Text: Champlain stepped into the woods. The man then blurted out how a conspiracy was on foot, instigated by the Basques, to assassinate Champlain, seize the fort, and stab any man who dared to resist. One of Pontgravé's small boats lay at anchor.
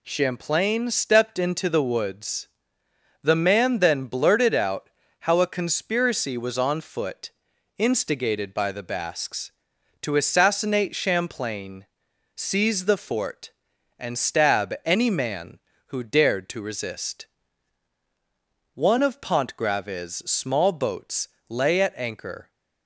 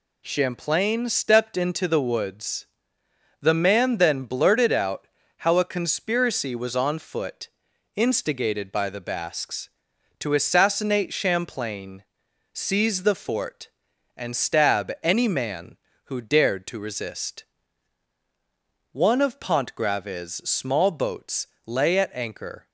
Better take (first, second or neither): neither